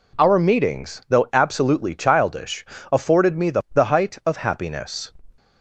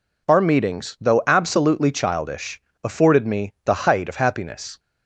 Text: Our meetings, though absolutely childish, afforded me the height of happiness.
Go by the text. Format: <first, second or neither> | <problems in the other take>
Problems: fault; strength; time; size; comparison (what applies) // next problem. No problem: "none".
second | says "the" twice; at 3.7 s